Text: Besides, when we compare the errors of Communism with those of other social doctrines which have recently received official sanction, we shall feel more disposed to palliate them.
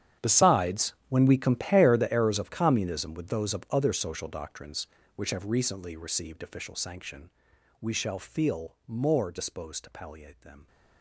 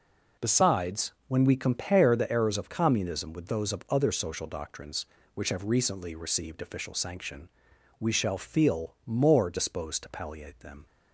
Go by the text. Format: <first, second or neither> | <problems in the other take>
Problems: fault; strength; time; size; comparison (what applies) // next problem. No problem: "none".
second | gets quieter; strong; throughout; 18.5 dB